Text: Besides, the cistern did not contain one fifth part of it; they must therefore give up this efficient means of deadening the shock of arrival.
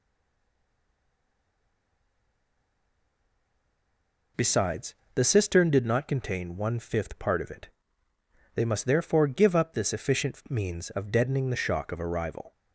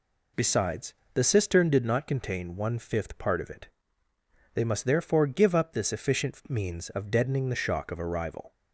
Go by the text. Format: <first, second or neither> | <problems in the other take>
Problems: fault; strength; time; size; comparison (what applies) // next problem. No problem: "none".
second | stays silent before the first word; strong; until 4.3 s; 4.3 s long